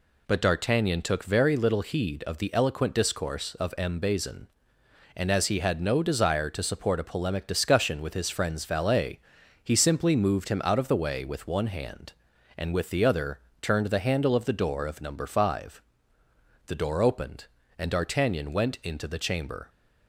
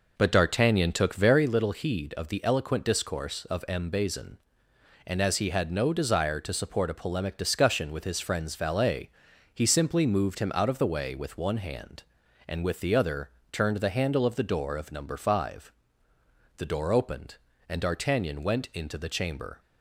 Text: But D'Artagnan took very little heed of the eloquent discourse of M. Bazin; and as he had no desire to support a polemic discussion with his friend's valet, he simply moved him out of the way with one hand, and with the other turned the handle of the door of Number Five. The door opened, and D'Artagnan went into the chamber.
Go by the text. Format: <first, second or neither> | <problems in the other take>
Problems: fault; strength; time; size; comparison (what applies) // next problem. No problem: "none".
first | starts louder than the rest; noticeable; until 1.5 s; 4.5 dB // pauses between "other" and "turned"; slight; at 13.2 s; 0.22 s long; slight in the first